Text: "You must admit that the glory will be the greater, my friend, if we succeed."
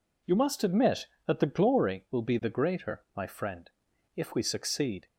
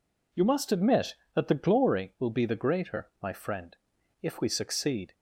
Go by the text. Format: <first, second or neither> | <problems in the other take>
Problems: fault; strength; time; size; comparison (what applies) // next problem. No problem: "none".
neither | none